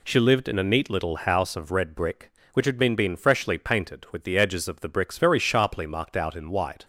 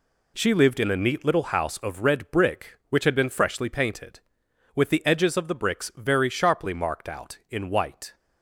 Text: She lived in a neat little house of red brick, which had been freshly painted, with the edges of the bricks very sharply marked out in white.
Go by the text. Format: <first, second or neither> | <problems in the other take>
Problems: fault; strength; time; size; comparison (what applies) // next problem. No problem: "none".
second | says "been" twice; at 2.9 s